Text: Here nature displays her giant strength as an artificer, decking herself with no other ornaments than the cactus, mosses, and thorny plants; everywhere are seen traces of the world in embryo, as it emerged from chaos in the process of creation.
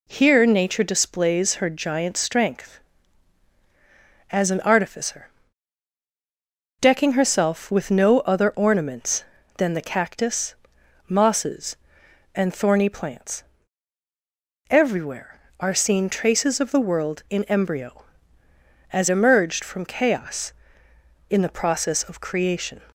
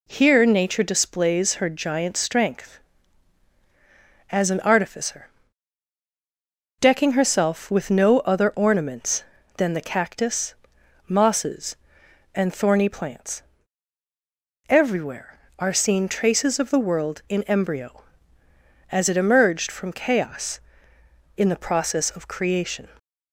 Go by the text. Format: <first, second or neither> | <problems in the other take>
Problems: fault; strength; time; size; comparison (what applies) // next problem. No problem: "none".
second | skips "it"; at 19.0 s